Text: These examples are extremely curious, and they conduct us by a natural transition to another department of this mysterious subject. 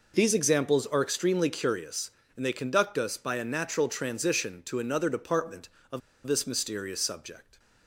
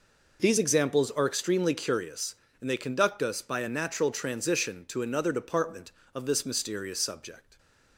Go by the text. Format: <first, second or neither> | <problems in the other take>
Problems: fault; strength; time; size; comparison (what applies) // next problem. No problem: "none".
second | pauses between "of" and "this"; slight; at 6.0 s; 0.26 s long